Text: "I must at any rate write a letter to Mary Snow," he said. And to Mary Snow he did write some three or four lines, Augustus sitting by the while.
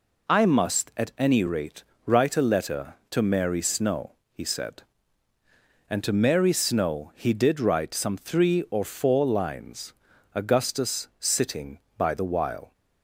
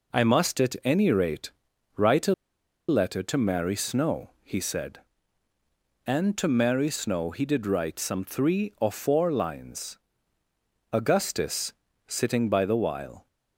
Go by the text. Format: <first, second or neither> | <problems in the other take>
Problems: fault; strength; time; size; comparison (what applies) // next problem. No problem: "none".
first | pauses between "rate" and "write"; at 1.5 s; 0.44 s long; slight in the first // pauses between "a" and "letter"; noticeable; at 2.3 s; 0.54 s long // pauses between "Augustus" and "sitting"; slight; at 11.7 s; 0.34 s long